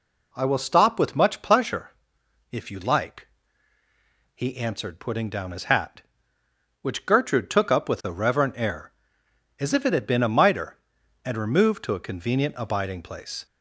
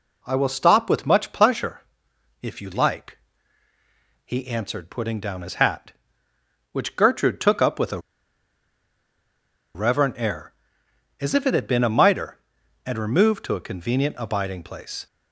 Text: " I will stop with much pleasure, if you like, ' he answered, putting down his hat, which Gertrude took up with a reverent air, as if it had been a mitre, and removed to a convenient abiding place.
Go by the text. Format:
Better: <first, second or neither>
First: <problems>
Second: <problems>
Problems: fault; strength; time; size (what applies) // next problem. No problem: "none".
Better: first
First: none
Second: pauses between "a" and "reverent"; strong; at 7.9 s; 1.7 s long